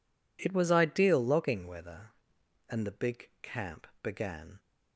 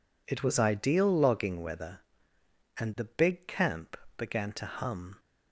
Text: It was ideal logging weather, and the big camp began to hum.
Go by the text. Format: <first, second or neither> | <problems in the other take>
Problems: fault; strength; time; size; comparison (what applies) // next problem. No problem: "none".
second | pauses between "camp" and "began"; slight; at 3.8 s; 0.16 s long; slight in the second // stops before "to hum"; at 4.5 s